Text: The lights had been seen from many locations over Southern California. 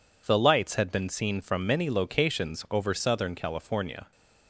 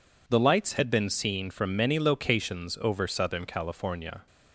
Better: neither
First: none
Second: none

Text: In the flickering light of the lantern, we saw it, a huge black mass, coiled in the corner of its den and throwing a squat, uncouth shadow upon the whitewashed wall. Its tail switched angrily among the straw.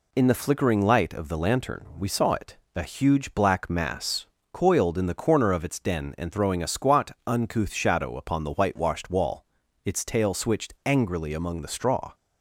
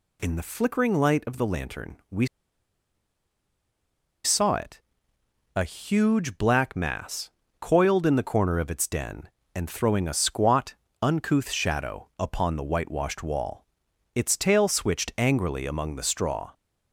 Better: first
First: none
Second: pauses between "we" and "saw"; strong; at 2.2 s; 1.9 s long

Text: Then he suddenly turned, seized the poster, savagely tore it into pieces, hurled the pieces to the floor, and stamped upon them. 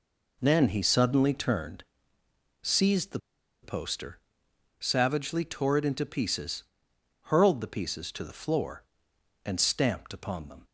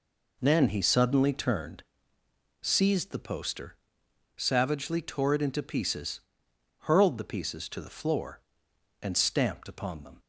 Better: second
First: pauses between "the" and "poster"; at 3.1 s; 0.44 s long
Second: none

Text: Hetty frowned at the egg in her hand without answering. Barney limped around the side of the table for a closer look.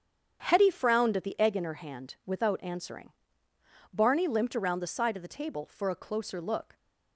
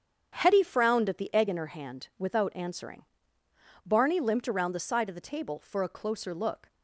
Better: neither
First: starts louder than the rest; strong; until 1.4 s; 7.5 dB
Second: starts louder than the rest; strong; until 1.3 s; 7.5 dB

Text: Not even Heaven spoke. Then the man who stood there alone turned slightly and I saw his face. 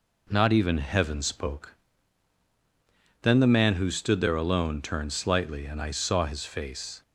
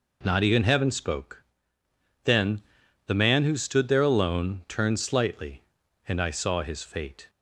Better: first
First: none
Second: pauses between "Then" and "the"; noticeable; at 2.6 s; 0.46 s long // says "fate" for "face"; at 6.8 s

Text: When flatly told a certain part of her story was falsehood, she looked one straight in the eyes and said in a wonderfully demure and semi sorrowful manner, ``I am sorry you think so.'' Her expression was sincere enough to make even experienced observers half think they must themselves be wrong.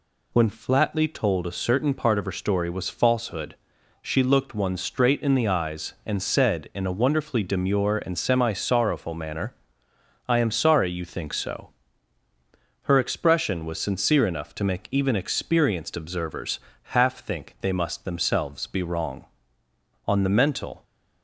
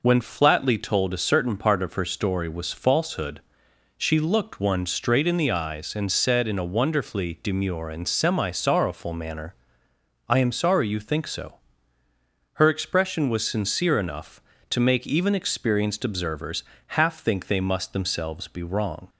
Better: second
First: pauses between "observers" and "half"; at 16.5 s; 0.38 s long // goes on to say "On the mental"; noticeable; from 20.0 s on; 0.76 s long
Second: pauses between "observers" and "half"; slight; at 16.6 s; 0.34 s long

